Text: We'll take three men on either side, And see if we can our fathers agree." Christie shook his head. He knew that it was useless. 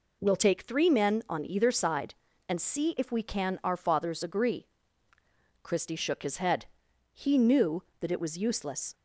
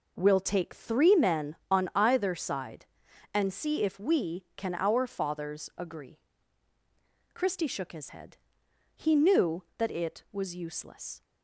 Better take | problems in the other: neither | none

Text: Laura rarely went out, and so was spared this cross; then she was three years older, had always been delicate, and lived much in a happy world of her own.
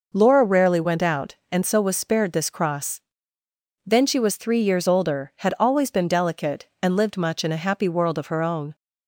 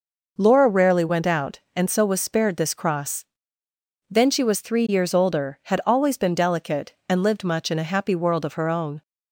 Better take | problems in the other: neither | none

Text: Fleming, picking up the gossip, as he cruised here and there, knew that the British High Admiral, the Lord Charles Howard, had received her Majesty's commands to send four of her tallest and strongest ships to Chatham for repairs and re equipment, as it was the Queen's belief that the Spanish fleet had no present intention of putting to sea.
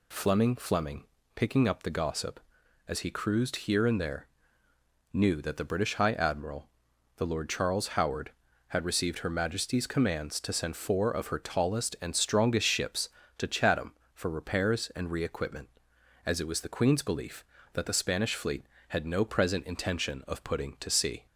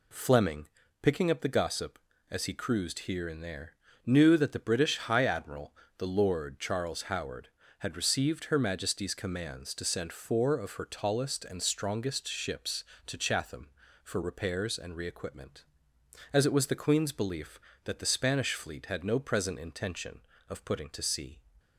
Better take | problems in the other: second | says "Fleming" twice; at 0.5 s

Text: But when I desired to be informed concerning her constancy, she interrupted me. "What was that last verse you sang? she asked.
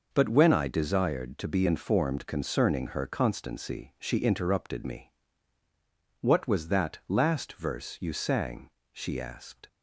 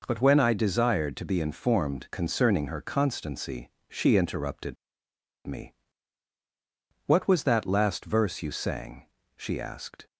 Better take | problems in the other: first | pauses between "interrupted" and "me"; noticeable; at 4.7 s; 0.70 s long

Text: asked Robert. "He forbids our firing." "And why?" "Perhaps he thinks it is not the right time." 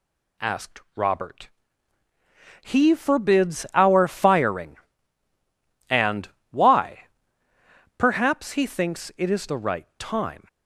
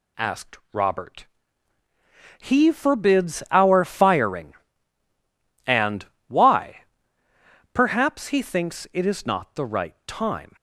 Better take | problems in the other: second | pauses between "And" and "why"; slight; at 6.2 s; 0.24 s long; slight in the second // skips "not"; at 9.4 s

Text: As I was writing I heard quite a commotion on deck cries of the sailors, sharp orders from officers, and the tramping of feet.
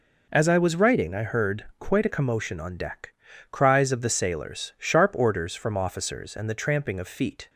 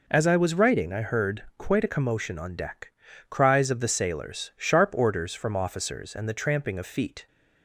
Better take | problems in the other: neither | pauses between "deck" and "cries"; the same in both

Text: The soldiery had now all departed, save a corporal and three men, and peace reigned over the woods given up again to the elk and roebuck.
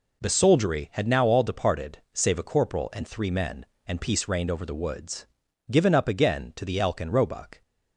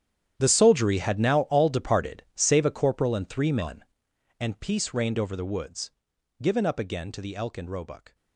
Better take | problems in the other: first | gets quieter; strong; throughout; 16.5 dB // pauses between "woods" and "given"; noticeable; at 5.9 s; 0.50 s long; noticeable in the first

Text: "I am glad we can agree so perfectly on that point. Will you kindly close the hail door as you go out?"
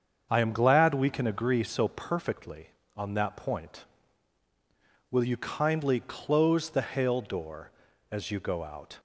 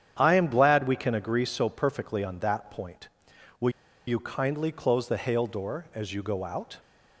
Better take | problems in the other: first | starts louder than the rest; strong; until 1.2 s; 9 dB; strong in the first // pauses between "Will" and "you"; at 3.6 s; 0.37 s long

